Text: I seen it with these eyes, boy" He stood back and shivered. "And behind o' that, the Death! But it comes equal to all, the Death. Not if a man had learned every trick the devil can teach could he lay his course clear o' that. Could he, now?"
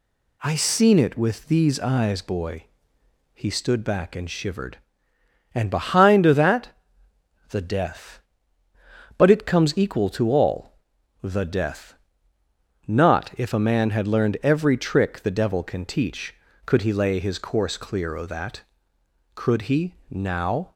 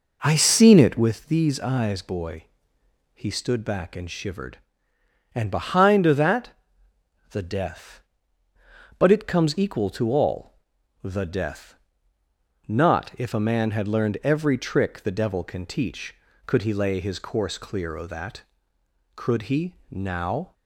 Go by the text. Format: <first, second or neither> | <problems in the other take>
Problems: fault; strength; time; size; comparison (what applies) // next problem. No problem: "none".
first | starts louder than the rest; noticeable; until 1.1 s; 5 dB // pauses between "boy" and "He"; noticeable; at 2.4 s; 0.70 s long; noticeable in the first